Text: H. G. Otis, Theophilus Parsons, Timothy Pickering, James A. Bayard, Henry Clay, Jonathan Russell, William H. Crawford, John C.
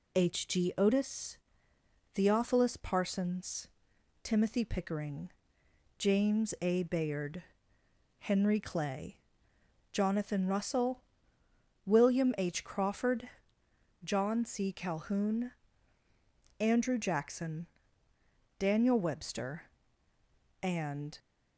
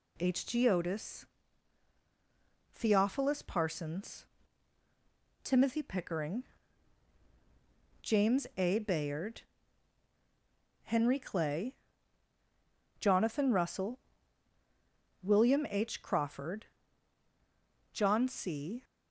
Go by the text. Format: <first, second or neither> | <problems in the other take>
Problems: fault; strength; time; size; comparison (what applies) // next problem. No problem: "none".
second | goes on to say "Calhoun Andrew Jackson Daniel Webster and"; strong; from 14.7 s on; 6.4 s long